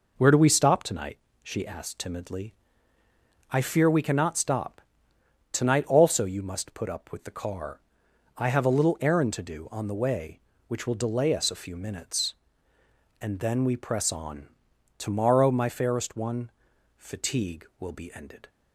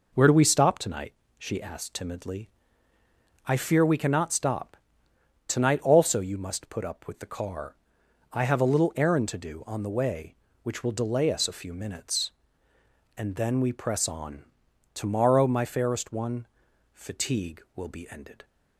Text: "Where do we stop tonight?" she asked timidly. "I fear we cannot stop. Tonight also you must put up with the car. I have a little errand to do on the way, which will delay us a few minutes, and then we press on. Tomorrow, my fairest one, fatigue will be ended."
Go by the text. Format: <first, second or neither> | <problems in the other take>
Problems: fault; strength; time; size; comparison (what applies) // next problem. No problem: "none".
neither | none